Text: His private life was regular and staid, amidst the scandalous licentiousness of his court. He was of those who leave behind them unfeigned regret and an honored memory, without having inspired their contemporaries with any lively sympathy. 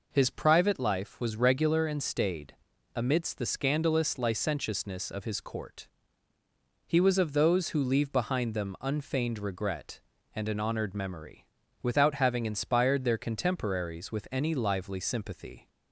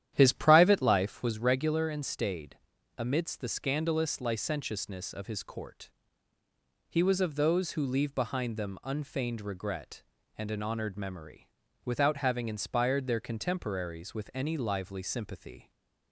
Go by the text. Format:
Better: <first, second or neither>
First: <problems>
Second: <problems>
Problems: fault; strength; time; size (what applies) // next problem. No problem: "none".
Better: first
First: none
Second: starts louder than the rest; strong; until 1.3 s; 11 dB // stays silent after the last word; slight; from 15.6 s on; 0.5 s long